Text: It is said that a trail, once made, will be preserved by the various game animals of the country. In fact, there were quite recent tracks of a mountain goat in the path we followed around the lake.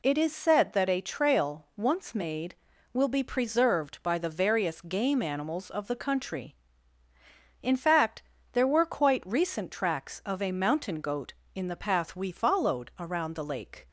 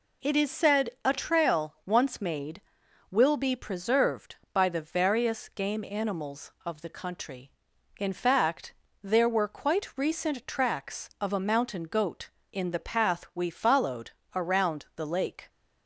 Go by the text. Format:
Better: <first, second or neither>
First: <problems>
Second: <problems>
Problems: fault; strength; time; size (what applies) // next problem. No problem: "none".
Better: first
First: none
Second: skips "that"; at 0.9 s // pauses between "followed" and "around"; slight; at 14.1 s; 0.24 s long